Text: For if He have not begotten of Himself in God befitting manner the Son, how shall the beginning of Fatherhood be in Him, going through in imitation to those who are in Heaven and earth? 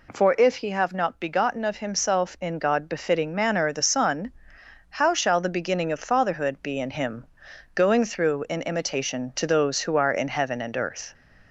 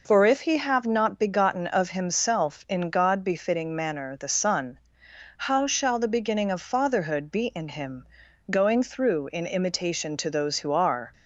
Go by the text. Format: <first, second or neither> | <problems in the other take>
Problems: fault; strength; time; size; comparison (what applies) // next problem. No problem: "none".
first | stops before "in Heaven and earth"; at 11.1 s